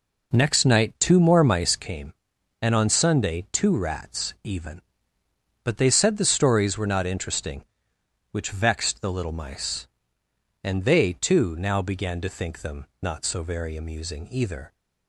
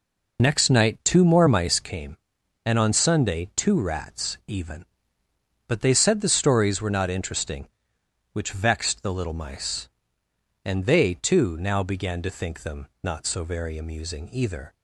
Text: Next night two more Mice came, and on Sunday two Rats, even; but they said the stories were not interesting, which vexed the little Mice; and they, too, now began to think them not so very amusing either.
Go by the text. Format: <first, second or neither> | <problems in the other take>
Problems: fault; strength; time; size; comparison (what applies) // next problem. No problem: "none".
first | loses the start of "Next"; at 0.3 s; 40 ms